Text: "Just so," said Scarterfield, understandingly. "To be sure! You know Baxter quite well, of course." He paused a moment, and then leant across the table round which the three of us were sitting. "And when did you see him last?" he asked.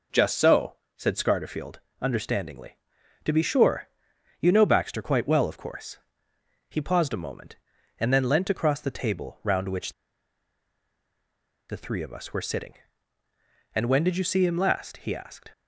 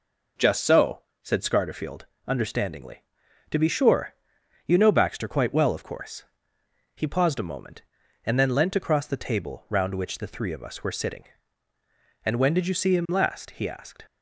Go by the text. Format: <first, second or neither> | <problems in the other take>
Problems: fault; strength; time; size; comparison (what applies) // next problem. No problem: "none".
second | pauses between "which" and "the"; strong; at 9.9 s; 1.7 s long